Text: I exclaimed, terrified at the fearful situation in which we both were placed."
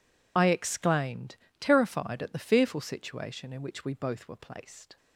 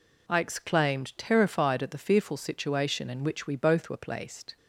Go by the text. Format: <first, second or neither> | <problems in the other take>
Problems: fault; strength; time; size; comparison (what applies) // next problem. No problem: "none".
second | loses the start of "I"; at 0.3 s; 35 ms